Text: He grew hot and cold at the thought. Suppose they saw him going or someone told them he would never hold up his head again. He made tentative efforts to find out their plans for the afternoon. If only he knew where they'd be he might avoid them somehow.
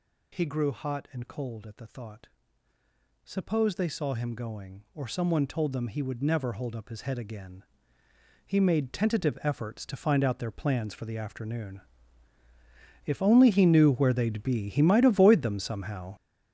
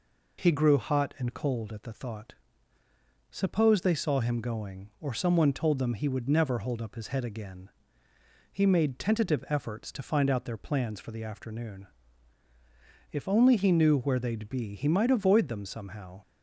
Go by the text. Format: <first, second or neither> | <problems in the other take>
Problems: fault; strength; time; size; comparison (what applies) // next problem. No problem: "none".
second | gets louder; strong; throughout; 10 dB